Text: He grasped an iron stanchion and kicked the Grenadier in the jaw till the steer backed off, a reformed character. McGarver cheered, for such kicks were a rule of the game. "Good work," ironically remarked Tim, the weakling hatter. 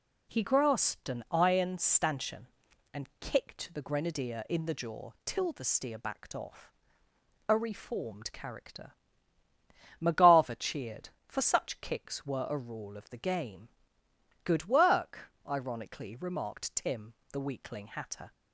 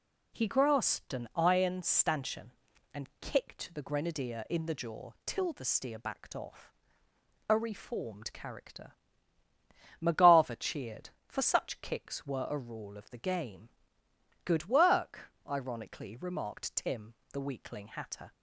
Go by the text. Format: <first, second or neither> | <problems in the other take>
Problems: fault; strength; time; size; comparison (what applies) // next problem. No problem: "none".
neither | none